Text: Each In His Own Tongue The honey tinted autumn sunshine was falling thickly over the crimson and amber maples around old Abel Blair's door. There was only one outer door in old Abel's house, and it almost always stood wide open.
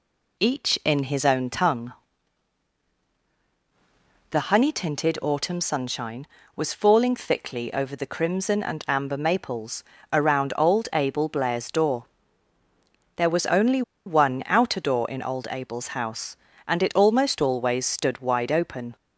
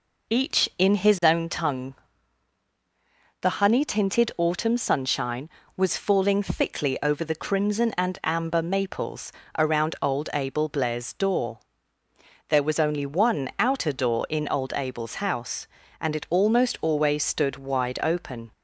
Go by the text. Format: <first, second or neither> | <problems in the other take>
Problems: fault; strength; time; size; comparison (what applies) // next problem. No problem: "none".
second | pauses between "Tongue" and "The"; strong; at 1.9 s; 2.3 s long; strong in the second // pauses between "maples" and "around"; slight; at 9.8 s; 0.30 s long; slight in the second // pauses between "only" and "one"; slight; at 13.8 s; 0.24 s long